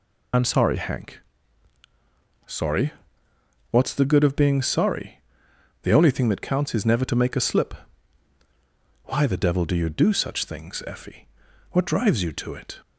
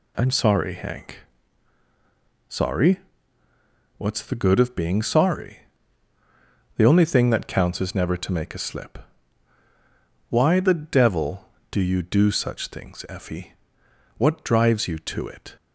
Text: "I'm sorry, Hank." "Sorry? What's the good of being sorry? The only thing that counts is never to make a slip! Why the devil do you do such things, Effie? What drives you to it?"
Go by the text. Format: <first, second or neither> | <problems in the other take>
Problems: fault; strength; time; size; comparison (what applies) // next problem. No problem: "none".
second | loses the start of "I'm"; at 0.3 s; 40 ms